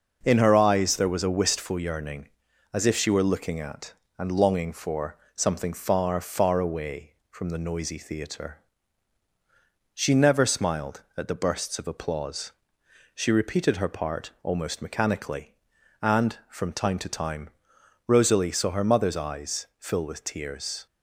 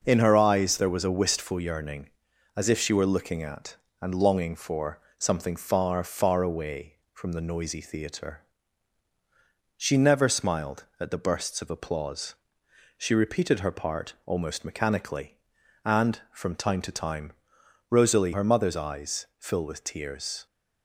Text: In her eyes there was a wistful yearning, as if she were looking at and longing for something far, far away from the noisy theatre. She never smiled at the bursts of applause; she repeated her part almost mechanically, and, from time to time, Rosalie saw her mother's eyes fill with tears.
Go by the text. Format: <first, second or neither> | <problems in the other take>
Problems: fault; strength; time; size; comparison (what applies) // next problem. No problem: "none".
first | pauses between "for" and "something"; slight; at 4.9 s; 0.18 s long; slight in the first // skips "saw"; at 18.3 s